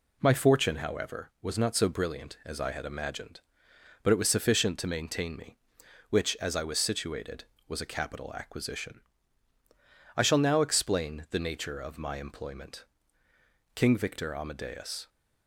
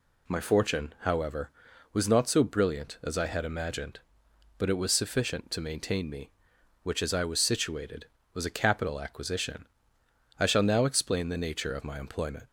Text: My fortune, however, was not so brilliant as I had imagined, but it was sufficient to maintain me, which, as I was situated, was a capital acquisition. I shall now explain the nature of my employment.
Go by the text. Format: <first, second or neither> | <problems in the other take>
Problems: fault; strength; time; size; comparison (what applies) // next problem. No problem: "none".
second | goes on to say "King Victor Amadeus"; from 13.7 s on; 1.3 s long